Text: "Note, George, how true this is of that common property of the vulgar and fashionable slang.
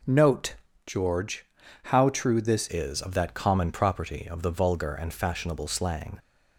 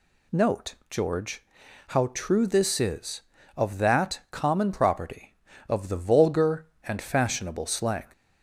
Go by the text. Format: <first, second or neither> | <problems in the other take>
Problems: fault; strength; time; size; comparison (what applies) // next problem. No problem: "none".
second | changes voice at "is"; from 2.6 s on; 3.5 s long